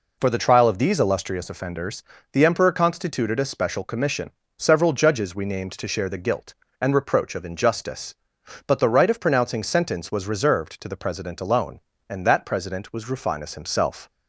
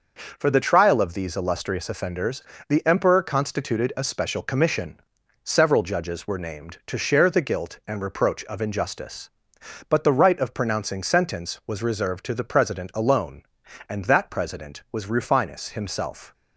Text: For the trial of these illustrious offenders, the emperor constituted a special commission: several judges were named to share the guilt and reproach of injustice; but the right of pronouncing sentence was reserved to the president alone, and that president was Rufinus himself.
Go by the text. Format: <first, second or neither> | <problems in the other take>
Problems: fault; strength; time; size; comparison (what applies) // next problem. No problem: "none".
second | says "we" for "were"; at 5.3 s